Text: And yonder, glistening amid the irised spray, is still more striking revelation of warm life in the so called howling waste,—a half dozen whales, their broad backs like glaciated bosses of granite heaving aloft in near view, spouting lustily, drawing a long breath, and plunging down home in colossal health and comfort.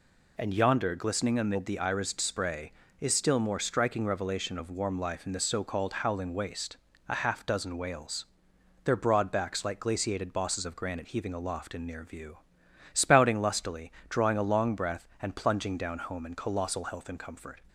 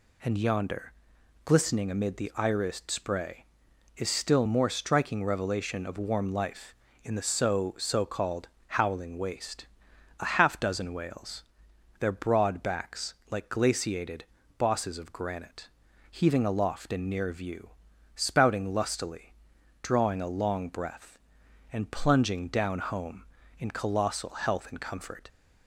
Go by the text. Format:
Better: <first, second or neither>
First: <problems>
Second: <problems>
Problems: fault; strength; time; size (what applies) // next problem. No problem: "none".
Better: first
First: none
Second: says "so" twice; at 7.7 s // pauses between "called" and "howling"; slight; at 8.4 s; 0.20 s long // pauses between "backs" and "like"; slight; at 13.1 s; 0.16 s long // pauses between "glaciated" and "bosses"; slight; at 14.2 s; 0.34 s long // pauses between "granite" and "heaving"; at 15.6 s; 0.42 s long